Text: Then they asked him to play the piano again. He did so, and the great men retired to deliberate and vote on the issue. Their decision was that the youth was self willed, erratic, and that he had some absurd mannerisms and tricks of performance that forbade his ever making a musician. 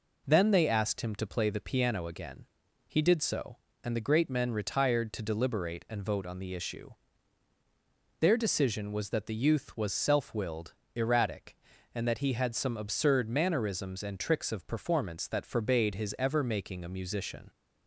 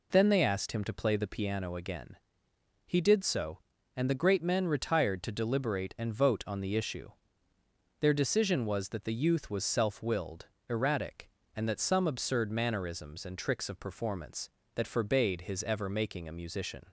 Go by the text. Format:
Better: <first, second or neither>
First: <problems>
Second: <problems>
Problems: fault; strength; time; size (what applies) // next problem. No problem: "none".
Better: first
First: none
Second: skips "he had"; at 11.7 s